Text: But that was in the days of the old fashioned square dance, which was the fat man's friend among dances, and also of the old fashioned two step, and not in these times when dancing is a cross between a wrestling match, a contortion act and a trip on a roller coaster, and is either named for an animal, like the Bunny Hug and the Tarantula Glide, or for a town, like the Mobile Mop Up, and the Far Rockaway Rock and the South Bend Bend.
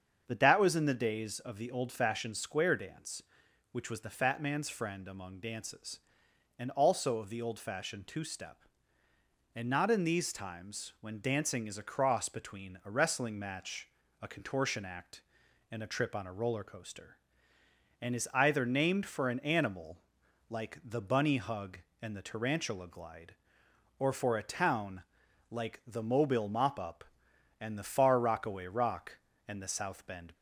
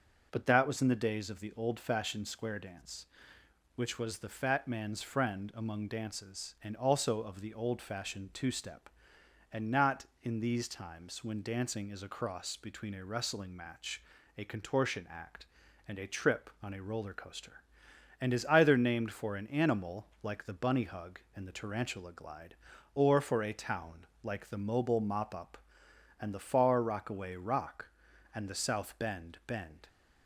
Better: second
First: starts louder than the rest; until 1.2 s; 7 dB // stops before "Bend"; at 30.3 s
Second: starts louder than the rest; until 1.3 s; 6.5 dB

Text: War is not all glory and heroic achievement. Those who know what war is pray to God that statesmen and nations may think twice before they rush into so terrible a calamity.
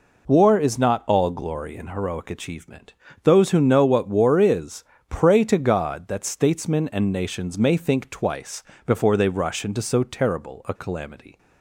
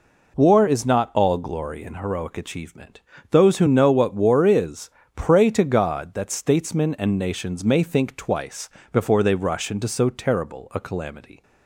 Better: neither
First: pauses between "is" and "pray"; slight; at 4.8 s; 0.26 s long // pauses between "twice" and "before"; slight; at 8.6 s; 0.22 s long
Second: pauses between "is" and "pray"; slight; at 4.8 s; 0.26 s long // pauses between "twice" and "before"; slight; at 8.7 s; 0.22 s long

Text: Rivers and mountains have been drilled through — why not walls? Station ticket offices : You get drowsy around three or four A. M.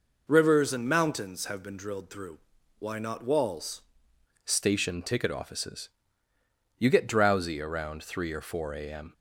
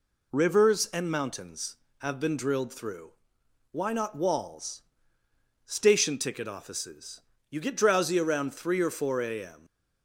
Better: second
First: changes voice at "Station"; from 4.4 s on; 4.7 s long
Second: none

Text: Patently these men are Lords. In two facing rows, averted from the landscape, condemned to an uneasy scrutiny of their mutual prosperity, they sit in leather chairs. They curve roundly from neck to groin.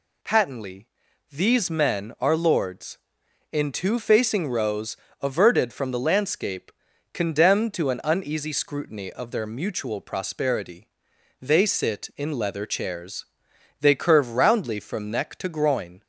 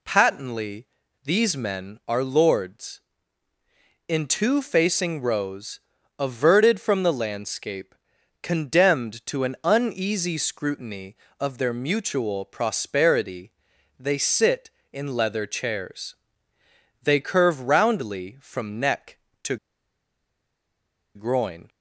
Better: first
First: pauses between "Patently" and "these"; at 0.8 s; 0.44 s long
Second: pauses between "Patently" and "these"; at 0.8 s; 0.38 s long // pauses between "to" and "groin"; strong; at 19.5 s; 1.5 s long

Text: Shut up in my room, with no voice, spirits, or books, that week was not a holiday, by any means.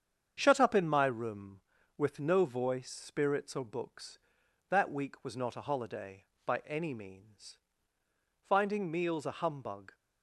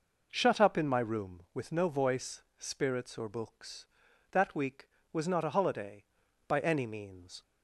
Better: second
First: starts louder than the rest; strong; until 1.3 s; 7.5 dB // goes on to say "Finding meals a humbug"; from 8.4 s on; 1.4 s long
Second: none

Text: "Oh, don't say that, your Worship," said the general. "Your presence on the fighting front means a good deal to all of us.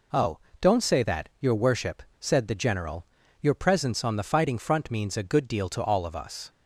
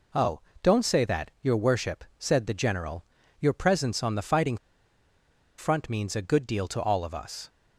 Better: first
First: none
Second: pauses between "fighting" and "front"; at 4.5 s; 1.0 s long

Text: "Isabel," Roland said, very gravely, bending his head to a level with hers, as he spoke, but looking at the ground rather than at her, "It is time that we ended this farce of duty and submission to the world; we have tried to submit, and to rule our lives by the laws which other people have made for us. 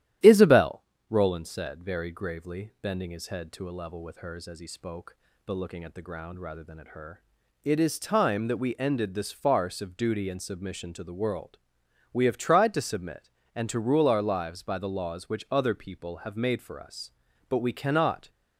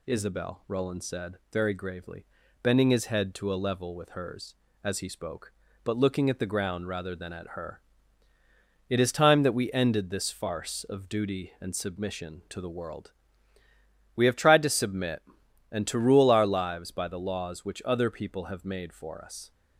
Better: second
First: starts louder than the rest; strong; until 1.4 s; 12.5 dB // goes on to say "But we cannot"; noticeable; from 17.4 s on; 0.80 s long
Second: none

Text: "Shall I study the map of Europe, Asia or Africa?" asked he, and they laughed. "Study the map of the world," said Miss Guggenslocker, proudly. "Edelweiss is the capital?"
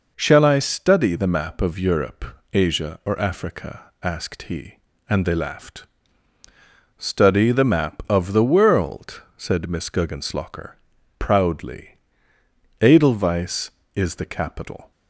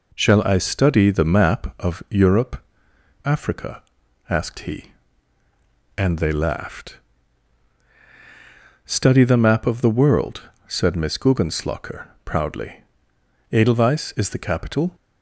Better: first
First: none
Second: skips "Asia or"; at 2.9 s

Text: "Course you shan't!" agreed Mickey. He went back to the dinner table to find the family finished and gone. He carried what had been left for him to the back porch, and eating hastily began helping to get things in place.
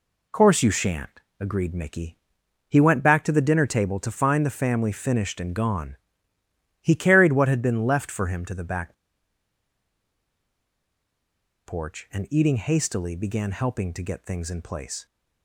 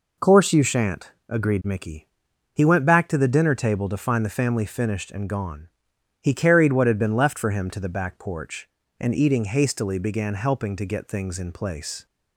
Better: second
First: pauses between "back" and "porch"; strong; at 8.9 s; 2.7 s long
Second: none

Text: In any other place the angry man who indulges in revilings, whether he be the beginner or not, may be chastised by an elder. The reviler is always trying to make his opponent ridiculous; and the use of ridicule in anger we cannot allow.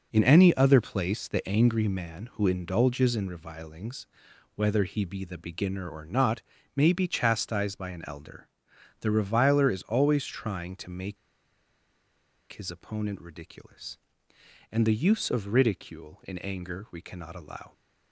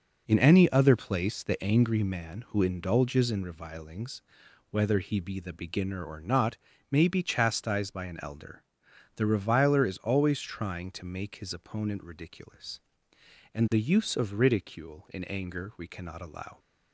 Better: second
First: pauses between "make" and "his"; strong; at 11.1 s; 1.3 s long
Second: none

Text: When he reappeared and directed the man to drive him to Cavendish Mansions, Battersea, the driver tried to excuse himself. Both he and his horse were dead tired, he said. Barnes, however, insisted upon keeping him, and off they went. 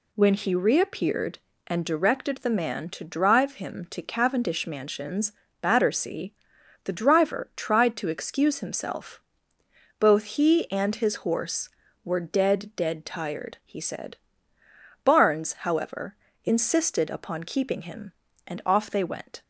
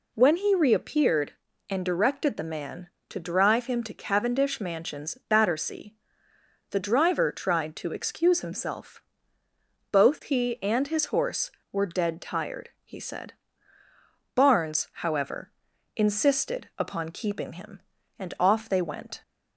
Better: second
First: says "dead" twice; at 12.7 s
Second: none

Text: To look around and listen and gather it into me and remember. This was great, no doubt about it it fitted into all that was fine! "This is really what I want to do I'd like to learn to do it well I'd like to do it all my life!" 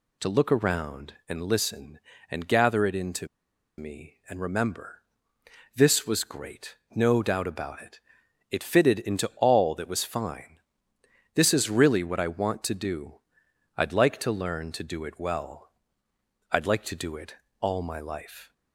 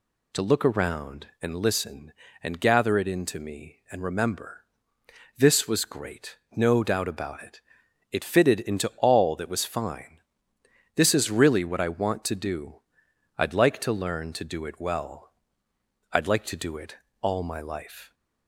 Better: second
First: pauses between "into" and "me"; noticeable; at 3.2 s; 0.51 s long // pauses between "it" and "it"; noticeable; at 8.0 s; 0.48 s long // pauses between "do" and "I'd"; noticeable; at 13.1 s; 0.58 s long // pauses between "well" and "I'd"; noticeable; at 15.6 s; 0.84 s long // pauses between "it" and "all"; slight; at 17.3 s; 0.24 s long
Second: pauses between "it" and "it"; noticeable; at 7.6 s; 0.48 s long // pauses between "do" and "I'd"; noticeable; at 12.7 s; 0.58 s long // pauses between "well" and "I'd"; noticeable; at 15.2 s; 0.84 s long // pauses between "it" and "all"; slight; at 16.9 s; 0.24 s long

